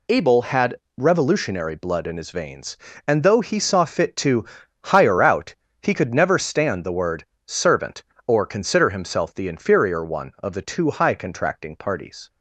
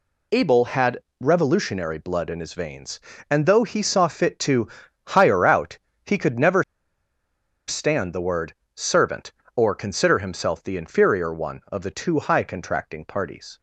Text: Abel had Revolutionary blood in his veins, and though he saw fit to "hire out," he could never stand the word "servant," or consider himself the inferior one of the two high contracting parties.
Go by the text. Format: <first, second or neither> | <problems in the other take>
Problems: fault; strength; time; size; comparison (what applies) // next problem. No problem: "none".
first | pauses between "had" and "Revolutionary"; slight; at 1.0 s; 0.18 s long; slight in the first // pauses between "to" and "hire"; at 4.6 s; 0.38 s long; also in the first // pauses between "never" and "stand"; at 6.6 s; 1.0 s long // pauses between "word" and "servant"; slight; at 8.5 s; 0.20 s long; slight in the first